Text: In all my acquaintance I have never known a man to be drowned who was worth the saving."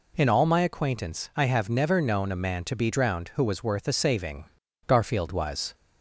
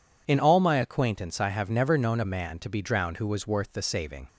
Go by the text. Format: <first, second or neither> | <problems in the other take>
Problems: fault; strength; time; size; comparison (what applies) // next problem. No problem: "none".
second | goes on to say "Garfield was"; noticeable; from 4.8 s on; 0.88 s long